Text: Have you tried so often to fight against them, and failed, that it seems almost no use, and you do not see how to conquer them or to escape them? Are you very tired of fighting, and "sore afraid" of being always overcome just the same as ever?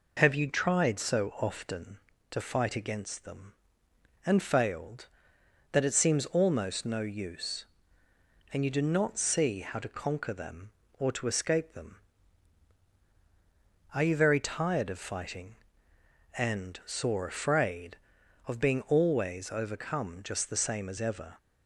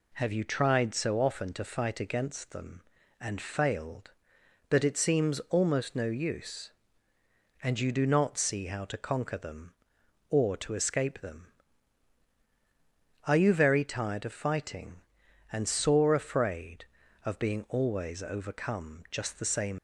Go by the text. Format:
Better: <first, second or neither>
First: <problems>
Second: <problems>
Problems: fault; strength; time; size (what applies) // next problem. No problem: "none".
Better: first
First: none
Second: stops before "as ever"; at 19.7 s